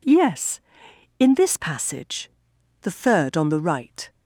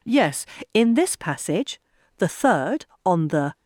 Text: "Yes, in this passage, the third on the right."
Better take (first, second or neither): first